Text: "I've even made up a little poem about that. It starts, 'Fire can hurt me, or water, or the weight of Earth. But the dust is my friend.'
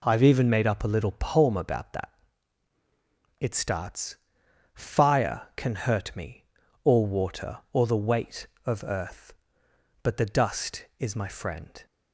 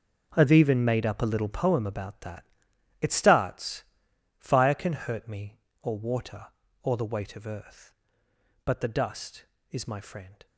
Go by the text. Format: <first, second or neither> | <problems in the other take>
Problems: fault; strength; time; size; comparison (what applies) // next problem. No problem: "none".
first | gets quieter; strong; throughout; 14 dB